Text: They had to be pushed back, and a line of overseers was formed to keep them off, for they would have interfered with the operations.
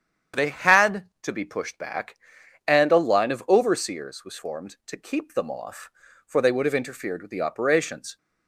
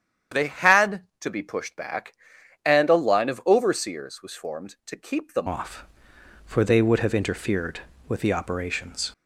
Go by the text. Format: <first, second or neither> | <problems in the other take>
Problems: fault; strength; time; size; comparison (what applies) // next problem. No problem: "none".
first | starts louder than the rest; strong; until 1.4 s; 9 dB; strong in the first // changes voice at "off"; from 5.4 s on; 3.7 s long